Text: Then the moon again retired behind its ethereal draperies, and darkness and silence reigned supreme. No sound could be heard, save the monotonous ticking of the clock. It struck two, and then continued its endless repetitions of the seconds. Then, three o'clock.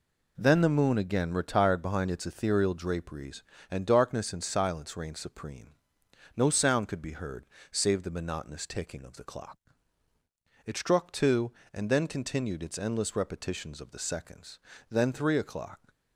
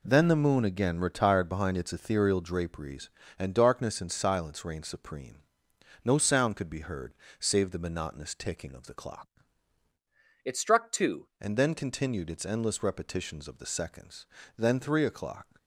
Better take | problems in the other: first | changes voice from "It" to "two"; from 10.4 to 11.2 s; 0.8 s long

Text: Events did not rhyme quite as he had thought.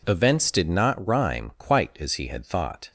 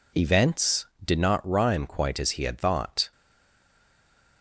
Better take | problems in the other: first | stays silent after the last word; noticeable; from 3.1 s on; 1.3 s long

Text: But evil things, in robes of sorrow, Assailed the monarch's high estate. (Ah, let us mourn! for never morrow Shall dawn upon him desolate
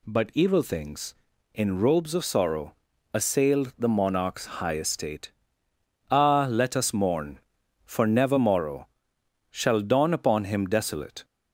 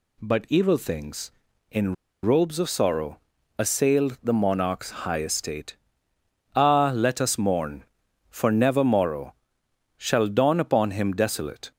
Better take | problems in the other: first | pauses between "in" and "robes"; slight; at 1.9 s; 0.29 s long // pauses between "morrow" and "Shall"; noticeable; at 9.3 s; 0.64 s long; noticeable in the first

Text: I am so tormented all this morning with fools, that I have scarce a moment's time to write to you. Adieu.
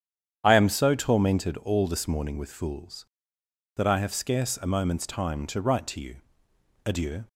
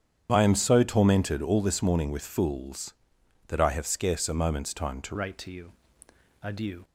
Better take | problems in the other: first | starts louder than the rest; strong; until 1.3 s; 8.5 dB; strong in the first // changes voice at "write"; from 5.1 s on; 1.7 s long

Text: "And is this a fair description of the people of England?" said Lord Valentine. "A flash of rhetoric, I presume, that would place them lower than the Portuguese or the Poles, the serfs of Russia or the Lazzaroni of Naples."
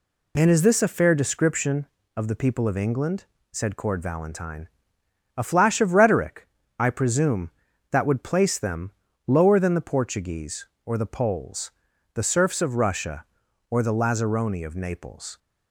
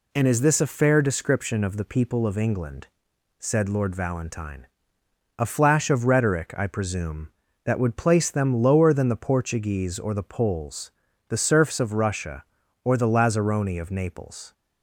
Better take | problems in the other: second | says "Cord" for "Lord"; at 3.7 s // pauses between "them" and "lower"; slight; at 8.9 s; 0.34 s long

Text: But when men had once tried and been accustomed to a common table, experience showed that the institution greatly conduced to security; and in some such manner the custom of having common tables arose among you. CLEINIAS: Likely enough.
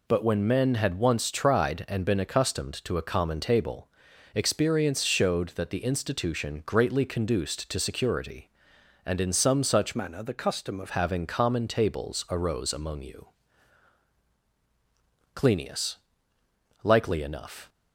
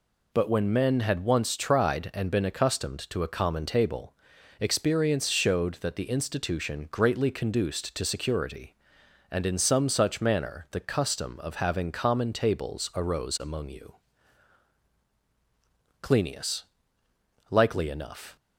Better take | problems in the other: second | changes voice from "manner" to "of"; from 9.9 to 10.8 s; 0.9 s long

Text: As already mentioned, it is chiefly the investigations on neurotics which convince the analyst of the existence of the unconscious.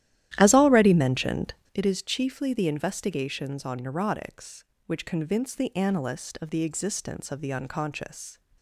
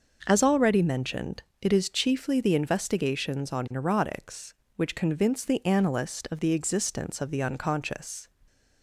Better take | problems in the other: second | starts louder than the rest; strong; until 1.8 s; 12.5 dB

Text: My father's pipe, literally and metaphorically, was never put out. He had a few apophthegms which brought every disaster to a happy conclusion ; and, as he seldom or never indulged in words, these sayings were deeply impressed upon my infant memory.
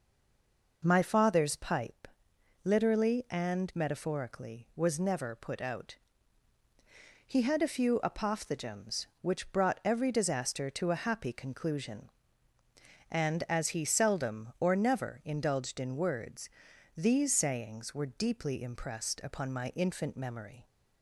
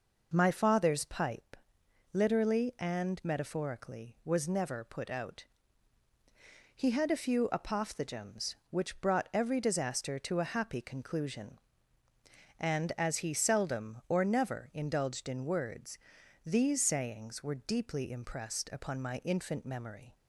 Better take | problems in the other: second | stays silent before the first word; slight; until 0.8 s; 0.8 s long

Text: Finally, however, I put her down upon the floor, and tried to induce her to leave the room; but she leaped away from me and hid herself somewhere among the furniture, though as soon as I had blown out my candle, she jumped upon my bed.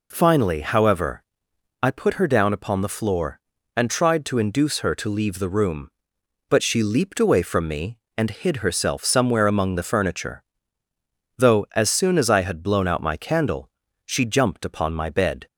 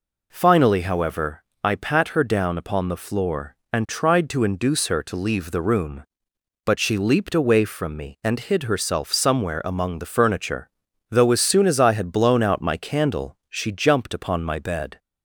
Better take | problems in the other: first | says "pat" for "put"; at 1.7 s

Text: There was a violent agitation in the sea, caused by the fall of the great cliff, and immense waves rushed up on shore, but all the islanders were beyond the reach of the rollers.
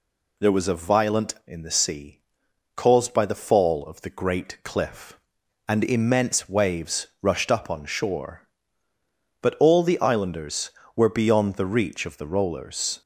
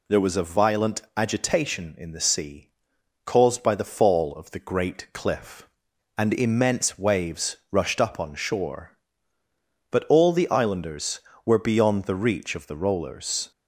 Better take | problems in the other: second | skips "agitation"; at 1.4 s

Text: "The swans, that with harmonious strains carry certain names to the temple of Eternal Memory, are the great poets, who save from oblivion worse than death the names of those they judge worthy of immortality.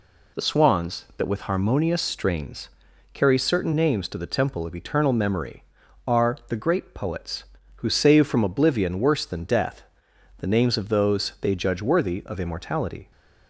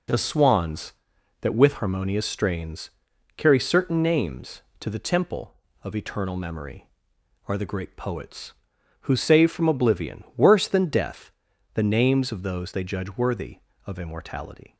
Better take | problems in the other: neither | pauses between "strains" and "carry"; noticeable; the same in both // pauses between "death" and "the"; noticeable; the same in both

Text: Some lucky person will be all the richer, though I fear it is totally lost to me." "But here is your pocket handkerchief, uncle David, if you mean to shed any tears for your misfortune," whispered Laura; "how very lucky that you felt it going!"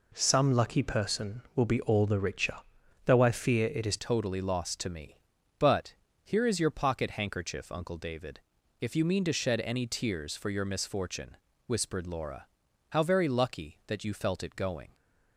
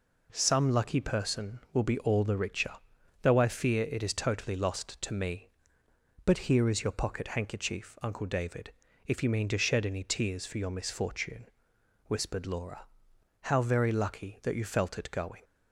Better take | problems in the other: second | changes voice at "totally"; from 3.9 s on; 11.0 s long // pauses between "But" and "here"; slight; at 5.9 s; 0.28 s long

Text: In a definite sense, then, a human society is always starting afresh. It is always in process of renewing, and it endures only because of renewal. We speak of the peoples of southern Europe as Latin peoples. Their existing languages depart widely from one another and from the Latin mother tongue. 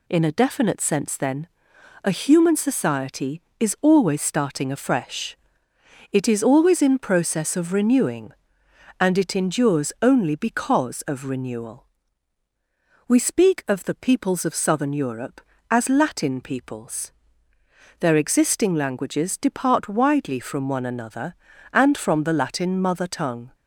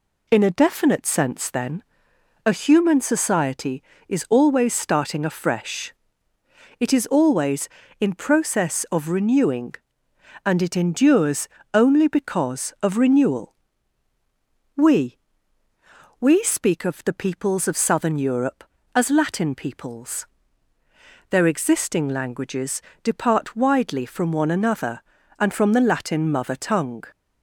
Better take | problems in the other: first | pauses between "endures" and "only"; slight; at 11.4 s; 0.26 s long // says "We" twice; at 16.1 s // pauses between "languages" and "depart"; slight; at 22.8 s; 0.20 s long

